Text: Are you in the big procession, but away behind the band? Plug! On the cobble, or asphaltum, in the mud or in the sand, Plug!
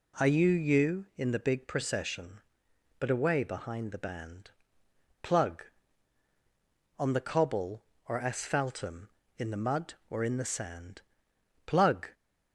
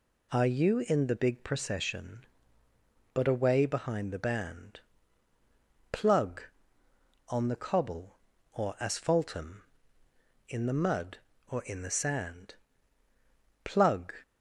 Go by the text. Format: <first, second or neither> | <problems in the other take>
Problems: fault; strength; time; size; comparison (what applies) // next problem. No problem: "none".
second | says "you" twice; at 0.4 s